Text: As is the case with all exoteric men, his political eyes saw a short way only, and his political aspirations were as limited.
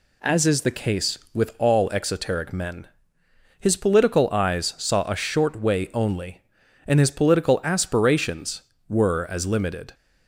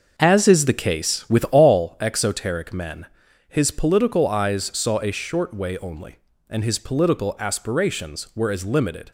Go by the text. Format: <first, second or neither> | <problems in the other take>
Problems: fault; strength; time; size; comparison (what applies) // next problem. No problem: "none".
first | starts louder than the rest; until 1.9 s; 6.5 dB